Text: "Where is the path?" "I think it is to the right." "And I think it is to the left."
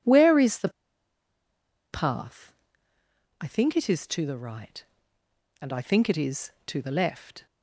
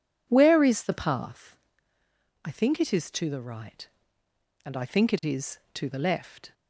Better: second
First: pauses between "the" and "path"; at 0.6 s; 1.2 s long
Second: none

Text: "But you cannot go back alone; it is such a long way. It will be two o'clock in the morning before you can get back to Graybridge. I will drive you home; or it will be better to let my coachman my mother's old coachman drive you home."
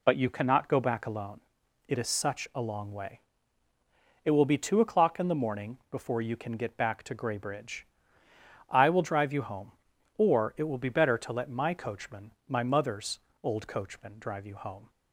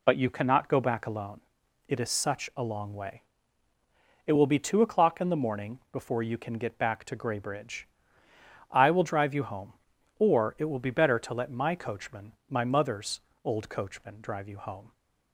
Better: neither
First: pauses between "coachman" and "my"; slight; at 12.3 s; 0.16 s long // pauses between "mother's" and "old"; slight; at 13.1 s; 0.24 s long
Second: pauses between "coachman" and "my"; slight; at 12.3 s; 0.16 s long // pauses between "mother's" and "old"; slight; at 13.2 s; 0.24 s long

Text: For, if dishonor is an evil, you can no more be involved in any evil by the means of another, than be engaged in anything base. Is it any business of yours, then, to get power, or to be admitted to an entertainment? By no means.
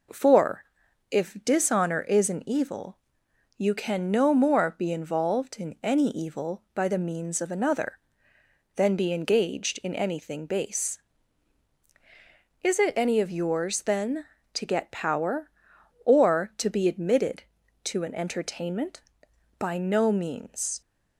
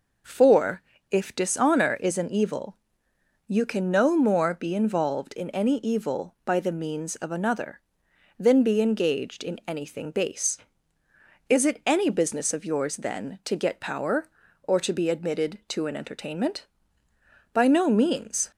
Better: second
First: skips "business"; at 13.2 s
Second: none

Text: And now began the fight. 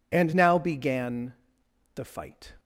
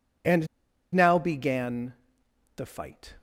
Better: first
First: pauses between "began" and "the"; noticeable; at 1.3 s; 0.62 s long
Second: pauses between "And" and "now"; noticeable; at 0.4 s; 0.48 s long // pauses between "began" and "the"; noticeable; at 1.9 s; 0.64 s long

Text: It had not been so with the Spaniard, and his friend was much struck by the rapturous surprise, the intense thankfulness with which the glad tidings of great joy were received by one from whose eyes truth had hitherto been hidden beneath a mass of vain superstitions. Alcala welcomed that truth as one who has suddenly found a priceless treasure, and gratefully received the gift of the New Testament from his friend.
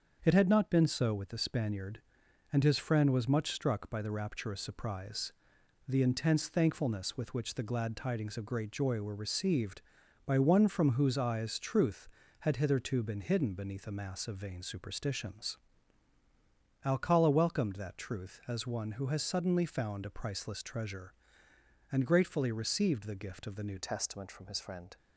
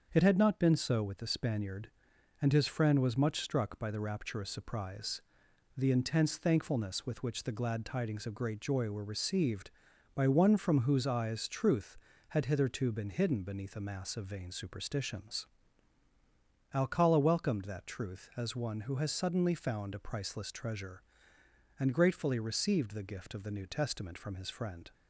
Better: second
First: starts louder than the rest; until 1.2 s; 7 dB // changes voice at "Testament"; from 23.7 s on; 1.2 s long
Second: starts louder than the rest; until 1.1 s; 7 dB

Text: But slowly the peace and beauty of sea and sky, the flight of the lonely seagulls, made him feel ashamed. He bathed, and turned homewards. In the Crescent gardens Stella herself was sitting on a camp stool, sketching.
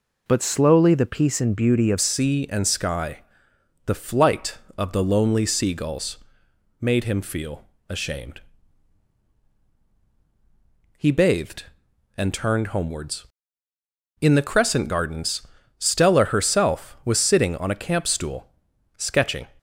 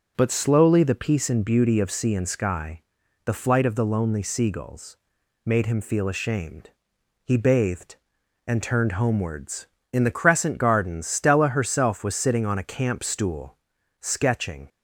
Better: second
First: changes voice at "sea"; from 2.0 s on; 17.4 s long // pauses between "feel" and "ashamed"; slight; at 7.6 s; 0.24 s long // pauses between "gardens" and "Stella"; slight; at 15.4 s; 0.32 s long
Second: none

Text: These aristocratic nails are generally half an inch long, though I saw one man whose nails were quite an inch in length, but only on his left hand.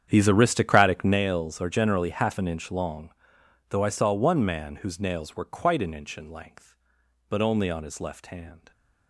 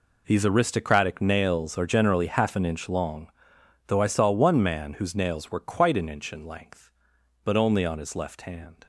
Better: second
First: starts louder than the rest; strong; until 1.2 s; 8.5 dB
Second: none

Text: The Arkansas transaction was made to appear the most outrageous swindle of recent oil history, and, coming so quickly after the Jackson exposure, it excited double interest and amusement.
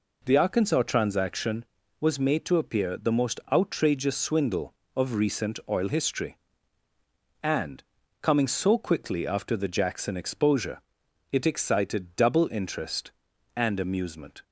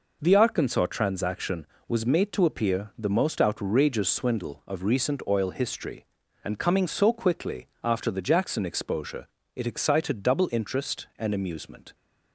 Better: neither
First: none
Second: none

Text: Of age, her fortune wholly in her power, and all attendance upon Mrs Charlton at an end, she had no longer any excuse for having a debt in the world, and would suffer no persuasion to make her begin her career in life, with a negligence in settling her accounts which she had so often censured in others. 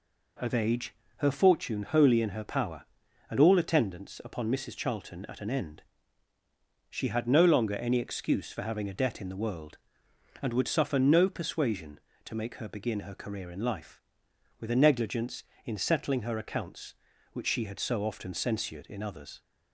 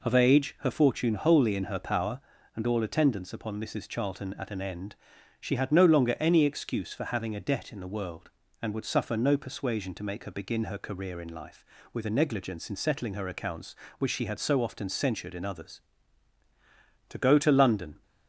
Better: first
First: none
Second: goes on to say "To go to London"; noticeable; from 17.0 s on; 0.94 s long

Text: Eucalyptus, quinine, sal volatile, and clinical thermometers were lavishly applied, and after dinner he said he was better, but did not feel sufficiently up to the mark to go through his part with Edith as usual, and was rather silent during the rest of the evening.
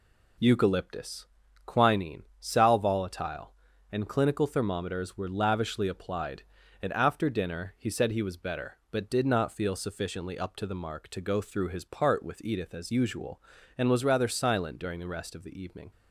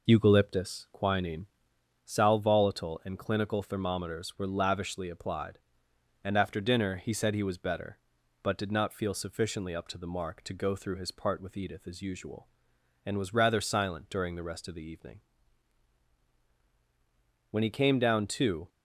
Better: first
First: none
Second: goes on to say "When he came down to"; noticeable; from 17.4 s on; 1.2 s long

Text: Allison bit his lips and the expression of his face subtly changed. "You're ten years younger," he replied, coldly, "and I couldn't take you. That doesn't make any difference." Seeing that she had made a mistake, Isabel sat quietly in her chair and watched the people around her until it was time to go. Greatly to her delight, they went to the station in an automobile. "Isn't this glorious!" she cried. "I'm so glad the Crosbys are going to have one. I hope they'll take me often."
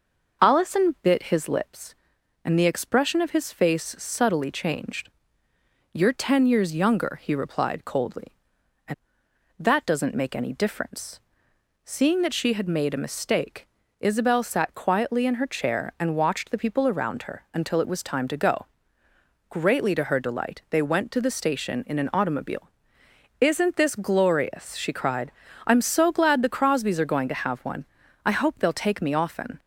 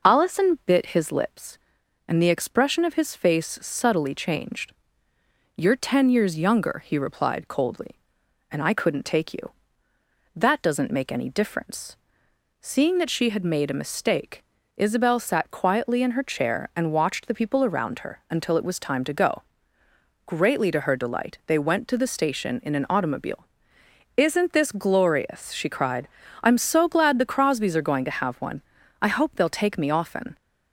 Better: second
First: skips "I couldn't take you"; at 9.2 s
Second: none

